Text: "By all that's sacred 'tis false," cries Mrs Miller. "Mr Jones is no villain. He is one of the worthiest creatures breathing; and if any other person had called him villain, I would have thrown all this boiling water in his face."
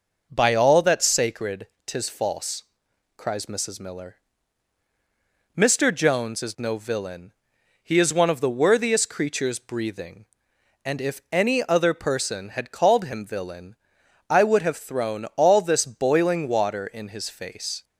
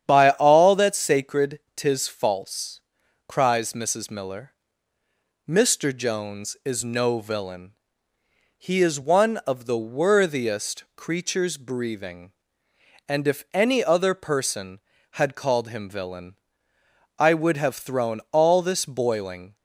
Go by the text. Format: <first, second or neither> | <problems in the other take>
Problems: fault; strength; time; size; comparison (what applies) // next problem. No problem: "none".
first | starts louder than the rest; strong; until 1.0 s; 9 dB // pauses between "sacred" and "tis"; slight; at 1.5 s; 0.16 s long; slight in the first // stops before "water in his face"; at 19.5 s